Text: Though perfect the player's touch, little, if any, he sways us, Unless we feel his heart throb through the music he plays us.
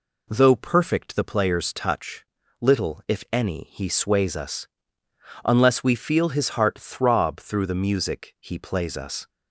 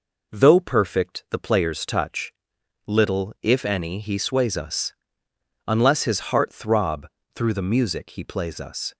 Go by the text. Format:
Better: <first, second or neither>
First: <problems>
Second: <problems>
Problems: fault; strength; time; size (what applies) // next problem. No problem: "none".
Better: first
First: none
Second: skips "we feel"; at 6.0 s // pauses between "throb" and "through"; slight; at 7.0 s; 0.28 s long